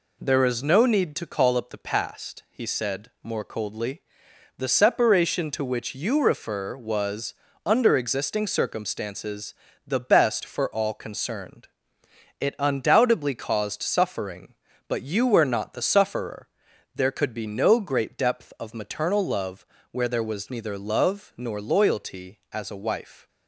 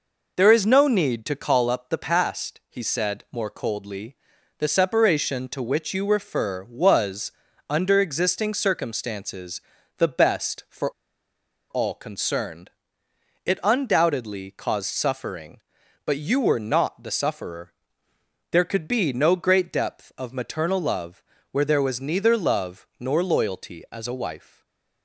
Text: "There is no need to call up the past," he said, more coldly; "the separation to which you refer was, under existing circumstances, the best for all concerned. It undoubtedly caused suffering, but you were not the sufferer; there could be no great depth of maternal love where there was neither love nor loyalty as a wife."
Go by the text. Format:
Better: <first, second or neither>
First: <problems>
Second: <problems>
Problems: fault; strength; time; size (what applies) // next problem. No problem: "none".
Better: first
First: pauses between "love" and "where"; slight; at 19.6 s; 0.24 s long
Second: pauses between "for" and "all"; noticeable; at 10.9 s; 0.79 s long // pauses between "love" and "where"; slight; at 21.2 s; 0.30 s long // stays silent after the last word; slight; from 24.3 s on; 0.7 s long